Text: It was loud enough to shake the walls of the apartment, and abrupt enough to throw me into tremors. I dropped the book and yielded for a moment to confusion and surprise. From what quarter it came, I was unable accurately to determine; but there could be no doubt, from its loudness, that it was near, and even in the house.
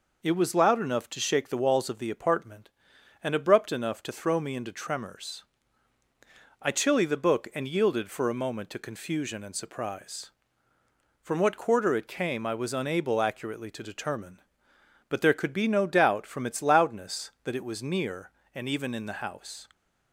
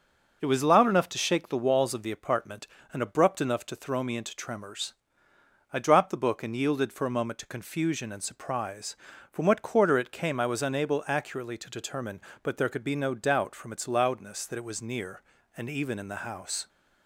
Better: second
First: says "chilly" for "dropped"; at 6.7 s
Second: none

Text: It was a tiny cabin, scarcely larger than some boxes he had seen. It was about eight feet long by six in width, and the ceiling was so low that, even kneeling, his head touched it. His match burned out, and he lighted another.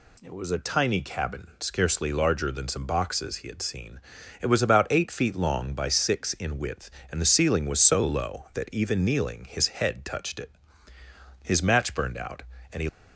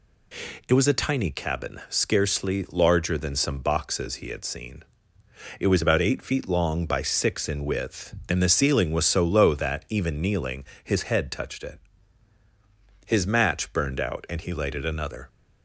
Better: second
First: stops before "lighted another"; at 12.8 s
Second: none

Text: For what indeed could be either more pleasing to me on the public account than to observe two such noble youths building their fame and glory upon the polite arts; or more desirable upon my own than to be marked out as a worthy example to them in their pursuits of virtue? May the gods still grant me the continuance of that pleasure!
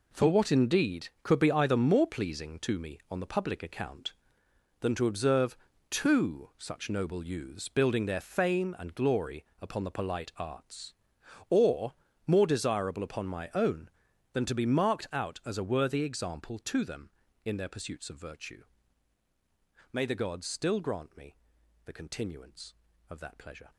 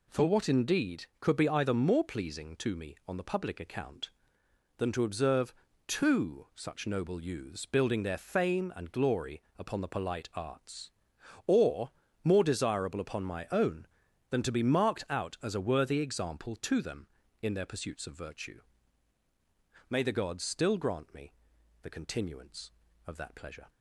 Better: second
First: gets quieter; strong; throughout; 10.5 dB // pauses between "observe" and "two"; slight; at 5.5 s; 0.34 s long // pauses between "glory" and "upon"; slight; at 9.4 s; 0.16 s long // pauses between "or" and "more"; slight; at 11.9 s; 0.32 s long // pauses between "me" and "the"; noticeable; at 21.3 s; 0.50 s long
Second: pauses between "observe" and "two"; slight; at 5.5 s; 0.34 s long // pauses between "glory" and "upon"; slight; at 9.4 s; 0.16 s long // pauses between "or" and "more"; slight; at 11.9 s; 0.32 s long // pauses between "me" and "the"; noticeable; at 21.3 s; 0.50 s long

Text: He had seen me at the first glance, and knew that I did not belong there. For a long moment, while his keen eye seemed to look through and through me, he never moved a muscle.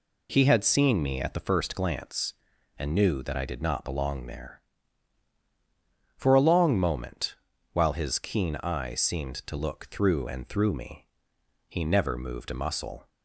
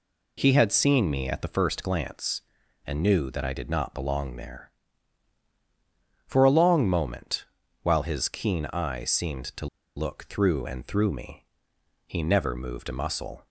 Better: first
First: none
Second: pauses between "to" and "look"; slight; at 9.6 s; 0.29 s long

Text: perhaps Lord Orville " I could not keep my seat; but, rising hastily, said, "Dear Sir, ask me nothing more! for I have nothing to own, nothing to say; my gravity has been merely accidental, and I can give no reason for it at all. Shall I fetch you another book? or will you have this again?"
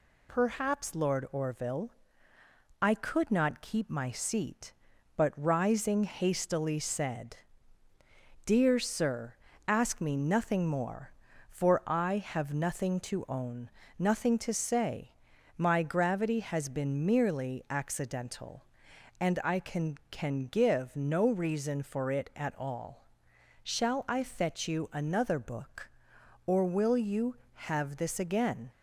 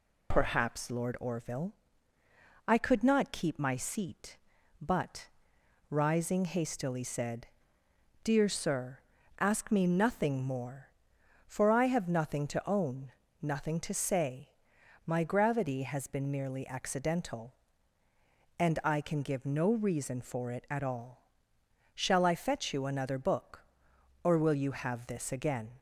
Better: second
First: says "can" twice; at 20.1 s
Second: none

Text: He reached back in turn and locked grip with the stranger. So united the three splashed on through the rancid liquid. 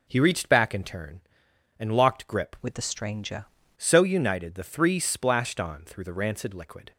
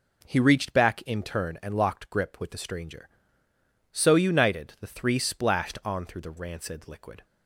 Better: second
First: changes voice from "with" to "stranger"; from 2.6 to 3.4 s; 0.8 s long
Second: none

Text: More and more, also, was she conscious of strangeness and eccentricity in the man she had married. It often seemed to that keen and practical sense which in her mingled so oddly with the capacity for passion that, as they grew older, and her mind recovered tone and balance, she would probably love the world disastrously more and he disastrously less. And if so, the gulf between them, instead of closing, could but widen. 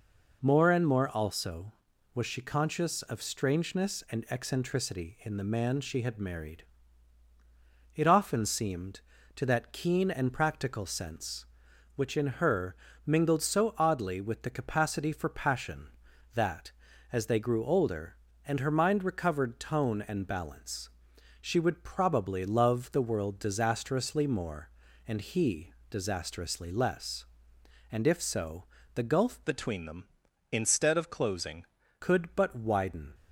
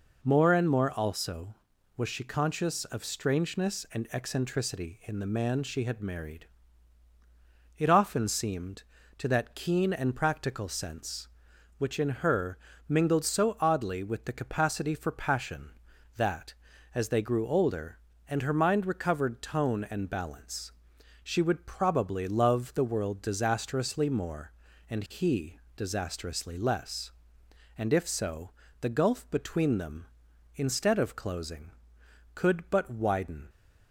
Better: second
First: pauses between "her" and "mingled"; slight; at 12.7 s; 0.32 s long // pauses between "he" and "disastrously"; slight; at 25.7 s; 0.16 s long // changes voice from "between" to "closing"; from 29.4 to 31.6 s; 2.2 s long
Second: pauses between "her" and "mingled"; slight; at 12.5 s; 0.32 s long // pauses between "he" and "disastrously"; slight; at 25.5 s; 0.16 s long

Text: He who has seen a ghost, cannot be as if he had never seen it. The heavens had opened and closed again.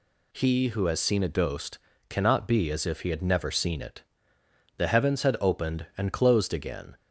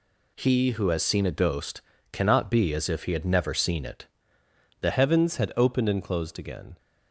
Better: first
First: none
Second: changes voice at "heavens"; from 4.9 s on; 1.8 s long

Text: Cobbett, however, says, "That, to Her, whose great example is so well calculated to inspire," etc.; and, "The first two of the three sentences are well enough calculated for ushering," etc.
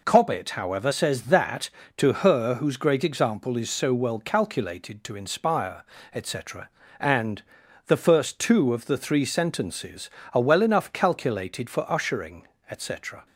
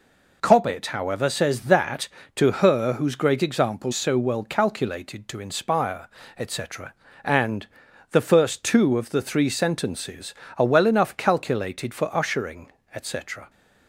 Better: first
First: none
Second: skips "is"; at 3.9 s

